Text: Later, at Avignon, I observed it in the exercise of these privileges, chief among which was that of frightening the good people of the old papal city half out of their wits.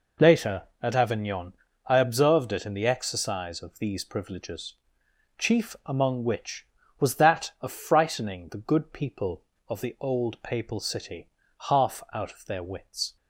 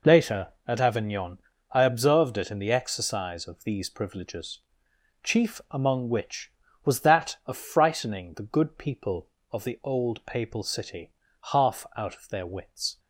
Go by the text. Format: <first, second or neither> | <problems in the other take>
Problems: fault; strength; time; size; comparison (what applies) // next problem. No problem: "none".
neither | pauses between "city" and "half"; the same in both